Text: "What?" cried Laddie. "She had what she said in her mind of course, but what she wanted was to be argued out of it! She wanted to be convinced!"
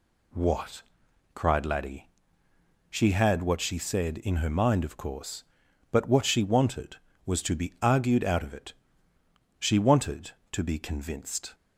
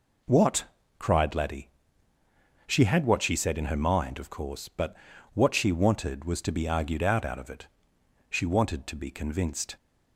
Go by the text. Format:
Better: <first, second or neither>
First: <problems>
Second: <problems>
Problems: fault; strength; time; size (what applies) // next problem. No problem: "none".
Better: first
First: none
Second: pauses between "but" and "what"; at 4.9 s; 0.38 s long // says "out" twice; at 7.2 s